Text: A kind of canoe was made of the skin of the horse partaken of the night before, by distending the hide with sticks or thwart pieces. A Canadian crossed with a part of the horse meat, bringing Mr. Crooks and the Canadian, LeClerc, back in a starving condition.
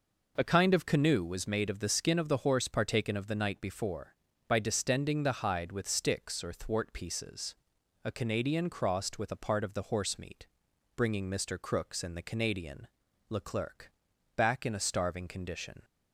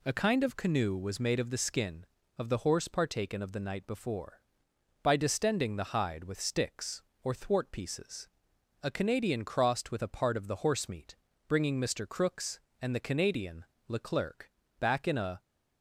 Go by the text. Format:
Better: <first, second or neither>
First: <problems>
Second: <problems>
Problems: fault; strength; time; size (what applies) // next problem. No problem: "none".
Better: first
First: none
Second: stops before "starving condition"; at 15.4 s